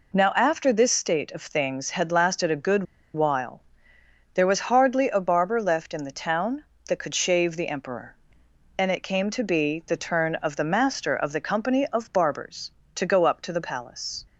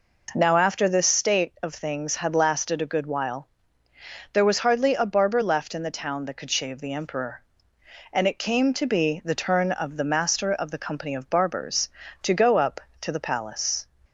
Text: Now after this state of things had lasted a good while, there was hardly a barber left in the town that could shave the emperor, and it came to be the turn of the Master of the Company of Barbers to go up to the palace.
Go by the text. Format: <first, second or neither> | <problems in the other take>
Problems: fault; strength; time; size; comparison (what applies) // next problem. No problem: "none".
second | pauses between "good" and "while"; slight; at 2.8 s; 0.31 s long